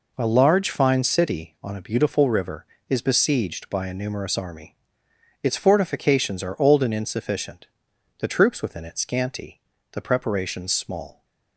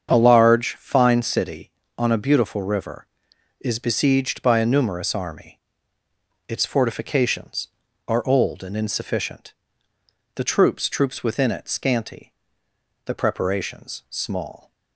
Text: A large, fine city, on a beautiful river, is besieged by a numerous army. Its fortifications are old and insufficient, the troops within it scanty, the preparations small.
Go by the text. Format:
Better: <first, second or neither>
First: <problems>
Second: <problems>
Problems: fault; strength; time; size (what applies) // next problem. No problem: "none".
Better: first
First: none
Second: starts louder than the rest; strong; until 1.1 s; 7.5 dB // says "troops" twice; at 10.8 s